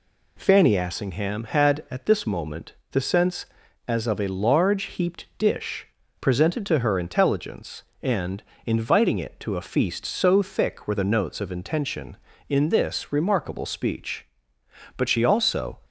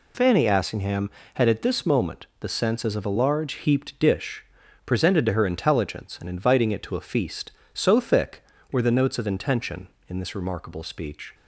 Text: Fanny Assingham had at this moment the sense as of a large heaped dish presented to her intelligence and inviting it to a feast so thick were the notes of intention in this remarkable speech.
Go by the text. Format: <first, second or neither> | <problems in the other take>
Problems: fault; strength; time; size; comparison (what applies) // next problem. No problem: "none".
second | pauses between "moment" and "the"; slight; at 2.7 s; 0.18 s long // pauses between "dish" and "presented"; slight; at 5.8 s; 0.32 s long; also in the second // pauses between "and" and "inviting"; slight; at 8.4 s; 0.22 s long // goes on to say "But she also"; noticeable; from 14.9 s on; 0.82 s long